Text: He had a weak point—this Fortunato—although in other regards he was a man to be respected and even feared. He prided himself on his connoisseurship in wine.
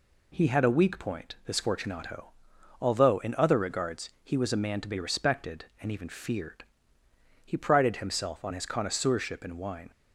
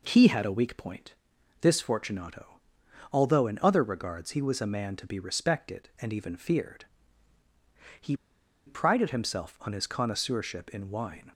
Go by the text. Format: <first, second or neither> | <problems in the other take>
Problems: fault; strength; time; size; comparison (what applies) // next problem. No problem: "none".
first | pauses between "He" and "prided"; noticeable; at 8.1 s; 0.52 s long